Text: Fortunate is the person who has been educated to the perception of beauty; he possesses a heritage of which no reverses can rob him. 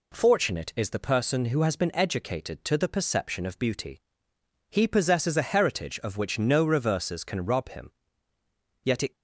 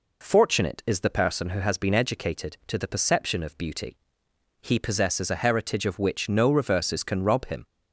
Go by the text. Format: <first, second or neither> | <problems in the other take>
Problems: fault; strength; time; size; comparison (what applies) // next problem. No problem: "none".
second | goes on to say "Yet it"; slight; from 8.8 s on; 0.32 s long